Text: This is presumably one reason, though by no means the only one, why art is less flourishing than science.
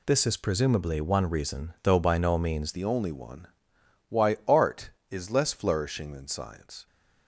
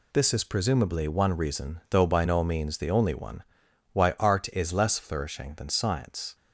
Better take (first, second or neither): second